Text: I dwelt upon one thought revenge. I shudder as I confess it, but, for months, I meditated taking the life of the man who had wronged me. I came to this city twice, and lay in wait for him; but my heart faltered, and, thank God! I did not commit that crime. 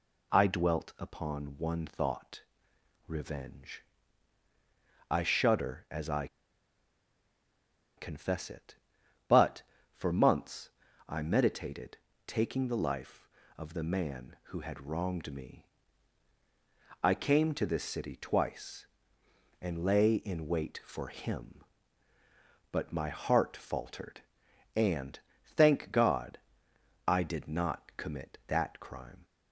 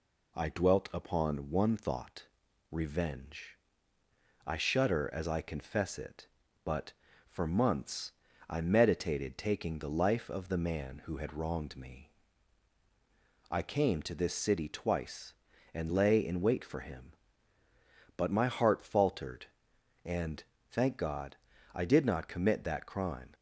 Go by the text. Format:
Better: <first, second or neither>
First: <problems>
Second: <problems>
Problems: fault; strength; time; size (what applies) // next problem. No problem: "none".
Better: second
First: pauses between "thought" and "revenge"; noticeable; at 2.4 s; 0.66 s long // pauses between "I" and "confess"; strong; at 6.2 s; 1.6 s long // pauses between "meditated" and "taking"; slight; at 11.9 s; 0.28 s long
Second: pauses between "thought" and "revenge"; at 2.2 s; 0.44 s long